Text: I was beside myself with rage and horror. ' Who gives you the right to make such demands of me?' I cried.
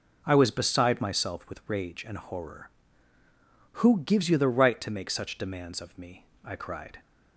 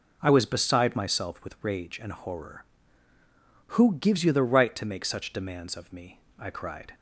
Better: neither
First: none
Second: none

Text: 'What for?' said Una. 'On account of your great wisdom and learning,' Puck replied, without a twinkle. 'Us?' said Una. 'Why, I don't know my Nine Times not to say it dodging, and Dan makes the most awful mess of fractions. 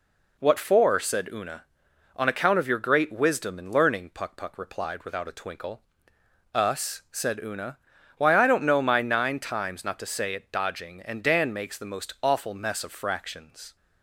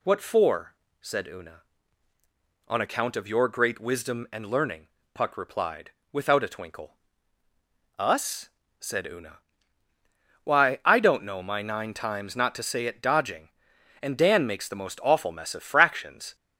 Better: second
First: says "Puck" twice; at 4.3 s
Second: none

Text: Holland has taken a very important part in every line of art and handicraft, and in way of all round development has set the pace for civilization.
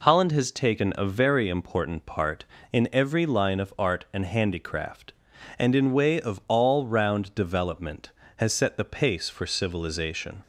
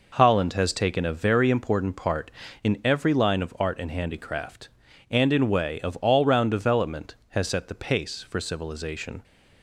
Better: neither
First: none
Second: none

